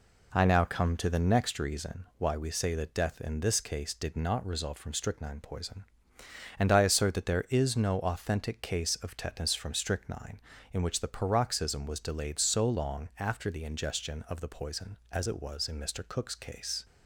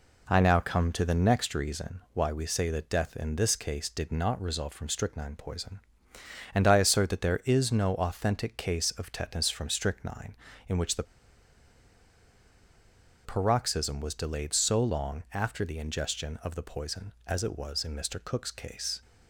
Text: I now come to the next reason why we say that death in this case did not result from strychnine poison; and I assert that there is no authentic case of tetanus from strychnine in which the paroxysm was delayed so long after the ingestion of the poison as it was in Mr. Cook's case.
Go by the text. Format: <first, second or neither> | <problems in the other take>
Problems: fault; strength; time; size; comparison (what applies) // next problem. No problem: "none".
first | pauses between "the" and "paroxysm"; strong; at 11.0 s; 2.2 s long